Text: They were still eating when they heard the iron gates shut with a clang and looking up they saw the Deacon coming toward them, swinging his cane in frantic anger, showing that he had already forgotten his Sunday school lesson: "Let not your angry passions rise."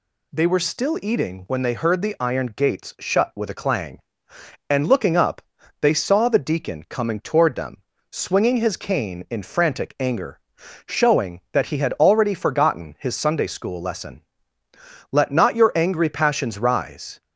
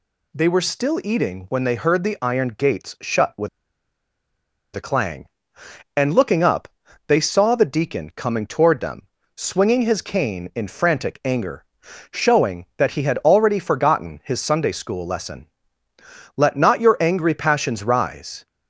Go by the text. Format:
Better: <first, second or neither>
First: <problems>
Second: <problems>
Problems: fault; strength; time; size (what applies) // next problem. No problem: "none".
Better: first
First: pauses between "up" and "they"; at 5.3 s; 0.42 s long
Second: pauses between "with" and "a"; strong; at 3.4 s; 1.2 s long // pauses between "up" and "they"; at 6.6 s; 0.42 s long